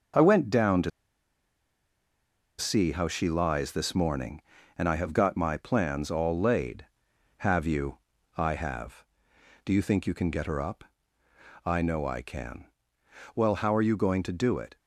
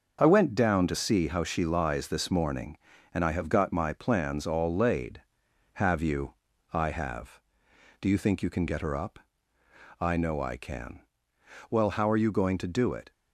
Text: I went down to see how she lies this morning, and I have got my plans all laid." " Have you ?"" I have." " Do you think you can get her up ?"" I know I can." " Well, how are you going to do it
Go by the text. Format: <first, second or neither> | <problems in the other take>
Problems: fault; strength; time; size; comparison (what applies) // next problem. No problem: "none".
second | starts louder than the rest; until 2.8 s; 7 dB; also in the second // pauses between "to" and "see"; strong; at 0.9 s; 1.6 s long